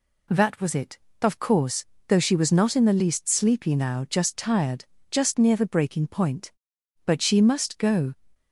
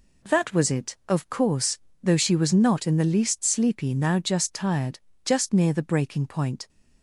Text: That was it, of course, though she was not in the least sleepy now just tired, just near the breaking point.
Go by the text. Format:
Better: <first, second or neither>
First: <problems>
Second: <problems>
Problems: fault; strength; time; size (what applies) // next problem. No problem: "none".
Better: second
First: goes on to say "But she must go"; noticeable; from 7.0 s on; 1.0 s long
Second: none